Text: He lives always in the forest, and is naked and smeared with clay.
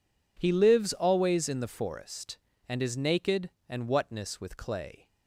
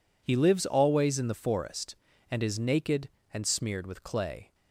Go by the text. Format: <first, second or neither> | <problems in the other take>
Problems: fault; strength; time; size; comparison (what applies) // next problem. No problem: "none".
second | says "whatness" for "smeared"; at 3.8 s